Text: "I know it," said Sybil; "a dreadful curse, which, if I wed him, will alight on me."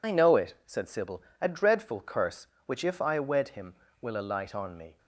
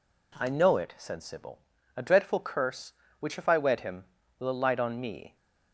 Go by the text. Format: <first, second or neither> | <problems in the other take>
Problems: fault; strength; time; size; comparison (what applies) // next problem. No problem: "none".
second | loses the start of "I"; at 0.0 s; 50 ms